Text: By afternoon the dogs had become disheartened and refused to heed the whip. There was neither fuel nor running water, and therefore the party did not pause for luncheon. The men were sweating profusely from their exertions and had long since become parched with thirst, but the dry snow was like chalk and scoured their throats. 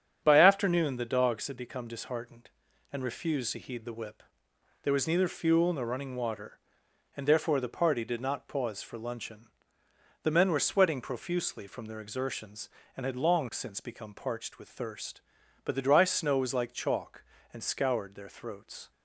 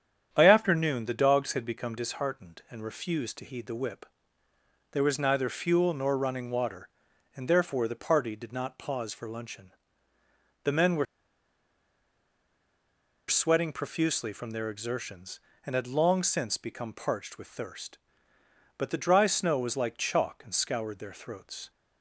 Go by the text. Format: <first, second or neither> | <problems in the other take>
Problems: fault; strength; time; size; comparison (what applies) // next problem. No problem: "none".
first | starts louder than the rest; strong; until 1.3 s; 8.5 dB; strong in the first // pauses between "were" and "sweating"; strong; at 11.0 s; 2.2 s long